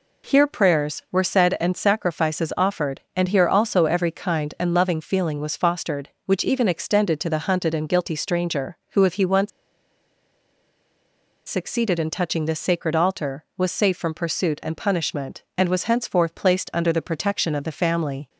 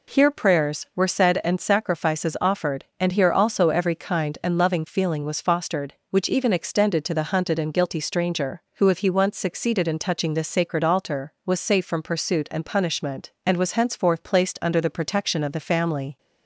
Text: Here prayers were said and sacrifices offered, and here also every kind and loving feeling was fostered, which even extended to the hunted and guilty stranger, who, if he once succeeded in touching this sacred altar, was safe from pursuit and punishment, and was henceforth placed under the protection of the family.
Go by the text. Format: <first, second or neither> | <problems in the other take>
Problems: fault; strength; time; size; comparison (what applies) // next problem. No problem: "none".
second | pauses between "once" and "succeeded"; strong; at 9.4 s; 1.9 s long